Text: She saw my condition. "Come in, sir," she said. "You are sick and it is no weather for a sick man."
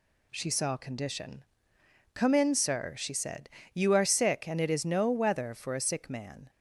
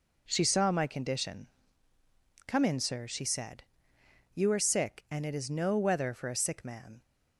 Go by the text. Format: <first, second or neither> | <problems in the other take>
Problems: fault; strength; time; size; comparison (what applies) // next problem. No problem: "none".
second | skips "my"; at 0.7 s